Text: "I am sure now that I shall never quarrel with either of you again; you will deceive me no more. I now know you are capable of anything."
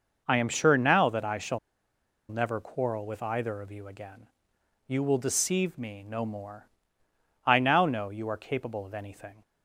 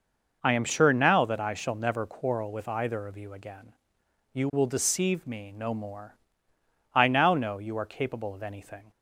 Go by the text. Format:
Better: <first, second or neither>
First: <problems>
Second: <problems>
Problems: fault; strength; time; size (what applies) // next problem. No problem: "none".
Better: second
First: pauses between "shall" and "never"; noticeable; at 1.5 s; 0.71 s long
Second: none